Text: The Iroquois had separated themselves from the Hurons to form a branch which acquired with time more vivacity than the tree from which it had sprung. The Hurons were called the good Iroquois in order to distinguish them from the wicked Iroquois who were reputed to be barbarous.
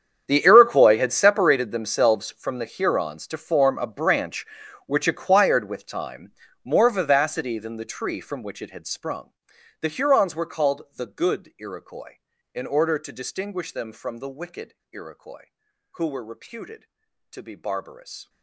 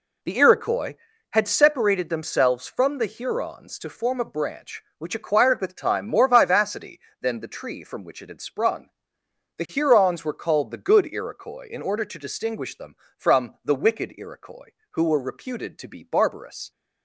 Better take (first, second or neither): second